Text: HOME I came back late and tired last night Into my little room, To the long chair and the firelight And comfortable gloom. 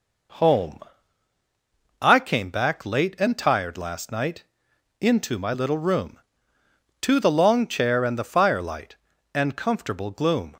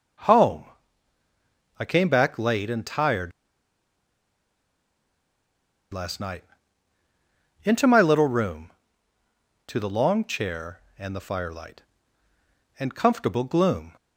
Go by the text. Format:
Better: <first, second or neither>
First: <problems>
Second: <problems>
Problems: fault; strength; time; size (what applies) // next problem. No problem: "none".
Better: first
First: pauses between "HOME" and "I"; at 0.7 s; 1.2 s long // pauses between "night" and "Into"; noticeable; at 4.4 s; 0.56 s long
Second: starts louder than the rest; strong; until 2.3 s; 7.5 dB // pauses between "HOME" and "I"; at 0.6 s; 1.1 s long // pauses between "tired" and "last"; strong; at 3.3 s; 2.6 s long // pauses between "night" and "Into"; at 6.4 s; 1.2 s long